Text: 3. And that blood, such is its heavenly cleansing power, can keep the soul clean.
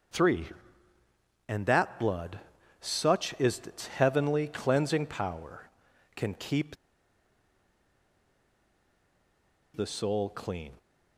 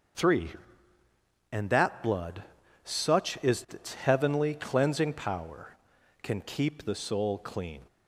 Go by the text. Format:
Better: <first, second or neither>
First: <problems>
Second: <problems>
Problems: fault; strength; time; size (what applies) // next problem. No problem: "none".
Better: second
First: starts louder than the rest; until 2.1 s; 6 dB // pauses between "keep" and "the"; strong; at 6.7 s; 2.9 s long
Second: starts louder than the rest; until 2.2 s; 6.5 dB